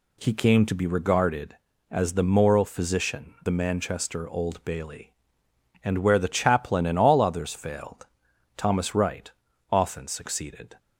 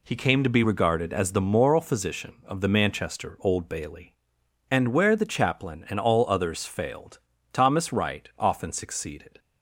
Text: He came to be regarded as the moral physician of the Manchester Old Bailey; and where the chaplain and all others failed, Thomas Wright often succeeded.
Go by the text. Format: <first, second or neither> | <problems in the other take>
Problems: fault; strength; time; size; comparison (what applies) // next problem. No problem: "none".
second | skips "of"; at 3.4 s // pauses between "Wright" and "often"; at 9.3 s; 0.40 s long